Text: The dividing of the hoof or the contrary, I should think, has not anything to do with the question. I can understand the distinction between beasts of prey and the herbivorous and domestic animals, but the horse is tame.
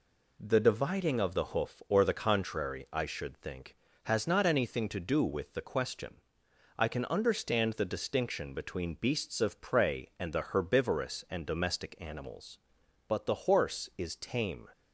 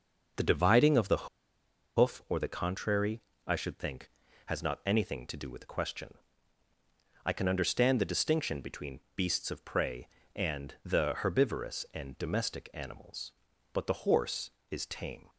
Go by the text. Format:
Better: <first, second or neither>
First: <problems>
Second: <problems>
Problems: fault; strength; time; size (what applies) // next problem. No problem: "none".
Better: first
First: none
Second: starts louder than the rest; noticeable; until 2.0 s; 6 dB // pauses between "the" and "hoof"; noticeable; at 1.2 s; 0.70 s long